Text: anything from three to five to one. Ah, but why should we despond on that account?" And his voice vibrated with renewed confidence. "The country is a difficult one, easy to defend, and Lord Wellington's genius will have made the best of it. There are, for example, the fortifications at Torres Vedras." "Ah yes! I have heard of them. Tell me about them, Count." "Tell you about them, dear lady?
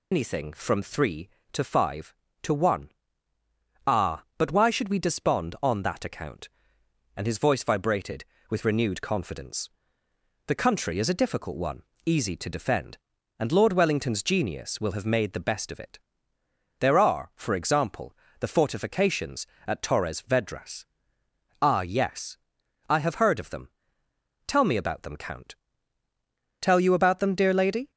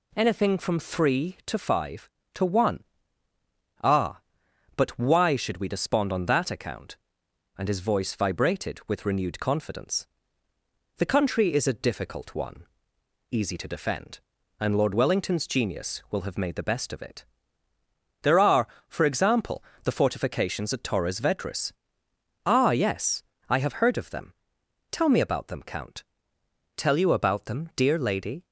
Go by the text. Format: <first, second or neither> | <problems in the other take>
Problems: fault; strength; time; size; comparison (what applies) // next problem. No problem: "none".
second | loses the start of "anything"; at 0.1 s; 80 ms